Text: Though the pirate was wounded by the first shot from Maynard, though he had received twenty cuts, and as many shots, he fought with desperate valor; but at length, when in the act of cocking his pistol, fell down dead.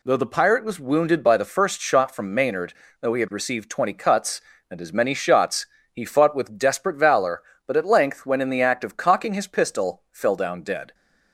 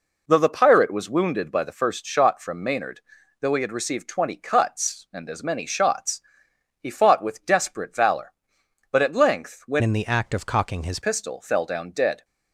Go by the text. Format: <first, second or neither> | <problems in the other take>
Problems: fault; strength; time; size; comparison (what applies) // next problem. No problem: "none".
first | changes voice from "in" to "his"; from 9.8 to 10.9 s; 1.1 s long